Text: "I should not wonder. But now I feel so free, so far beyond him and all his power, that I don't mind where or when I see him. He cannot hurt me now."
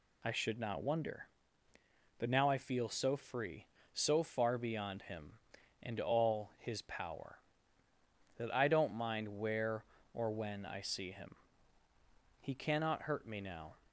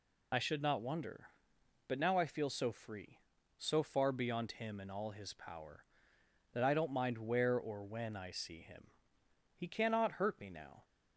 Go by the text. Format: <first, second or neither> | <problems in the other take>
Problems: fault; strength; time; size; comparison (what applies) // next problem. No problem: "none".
first | loses the start of "I"; at 0.3 s; 30 ms